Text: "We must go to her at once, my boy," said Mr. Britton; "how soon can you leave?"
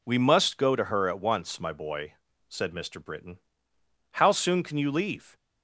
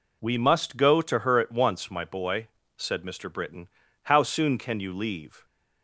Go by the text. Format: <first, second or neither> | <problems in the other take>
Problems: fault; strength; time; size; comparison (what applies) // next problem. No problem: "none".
neither | none